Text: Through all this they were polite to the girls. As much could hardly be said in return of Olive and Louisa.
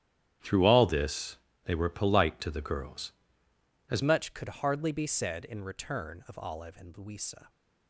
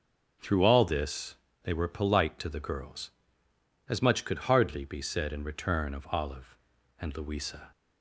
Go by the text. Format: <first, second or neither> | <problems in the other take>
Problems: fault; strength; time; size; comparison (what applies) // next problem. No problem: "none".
second | starts louder than the rest; strong; until 1.7 s; 10.5 dB // pauses between "this" and "they"; slight; at 1.3 s; 0.28 s long; slight in the second // changes voice at "much"; from 4.0 s on; 3.4 s long